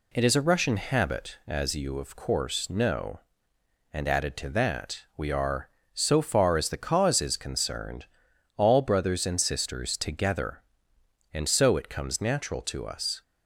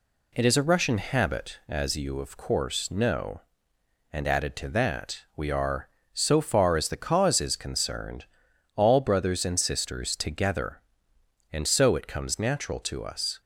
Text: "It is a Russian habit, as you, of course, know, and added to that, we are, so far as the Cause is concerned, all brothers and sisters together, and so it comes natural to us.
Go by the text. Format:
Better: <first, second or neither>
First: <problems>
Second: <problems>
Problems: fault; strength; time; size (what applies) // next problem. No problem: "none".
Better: neither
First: none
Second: none